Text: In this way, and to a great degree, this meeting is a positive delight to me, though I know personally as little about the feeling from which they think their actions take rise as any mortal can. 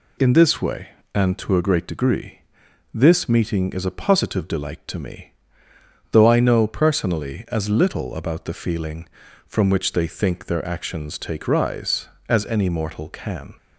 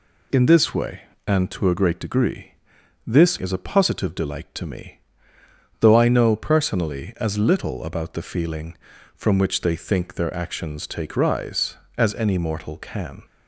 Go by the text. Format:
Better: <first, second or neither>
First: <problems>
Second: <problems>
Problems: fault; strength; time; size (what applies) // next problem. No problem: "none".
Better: first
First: none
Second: skips "meeting"; at 3.3 s